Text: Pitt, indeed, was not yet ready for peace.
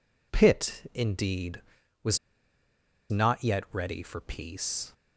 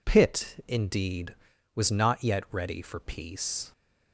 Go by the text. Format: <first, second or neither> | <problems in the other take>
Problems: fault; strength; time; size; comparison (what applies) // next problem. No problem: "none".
second | pauses between "was" and "not"; noticeable; at 2.1 s; 0.93 s long